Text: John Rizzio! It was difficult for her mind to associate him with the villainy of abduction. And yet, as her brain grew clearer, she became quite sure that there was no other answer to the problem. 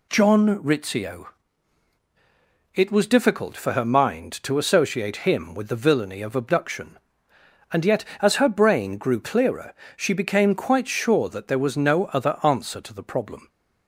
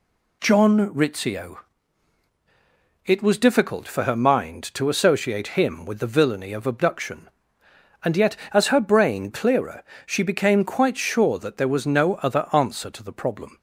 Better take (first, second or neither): first